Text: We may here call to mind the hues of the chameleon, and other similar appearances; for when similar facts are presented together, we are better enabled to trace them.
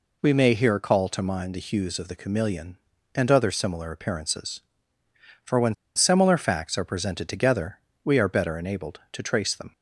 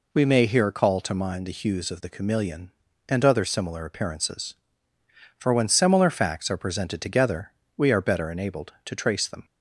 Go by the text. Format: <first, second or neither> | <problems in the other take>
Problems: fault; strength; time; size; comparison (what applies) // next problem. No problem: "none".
second | pauses between "when" and "similar"; slight; at 5.7 s; 0.21 s long